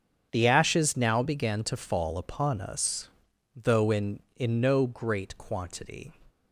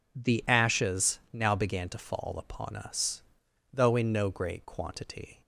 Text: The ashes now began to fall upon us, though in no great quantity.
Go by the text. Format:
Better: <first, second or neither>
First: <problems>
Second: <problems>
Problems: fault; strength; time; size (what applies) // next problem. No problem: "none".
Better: second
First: starts louder than the rest; strong; until 1.3 s; 8 dB // says "in" twice; at 4.3 s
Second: none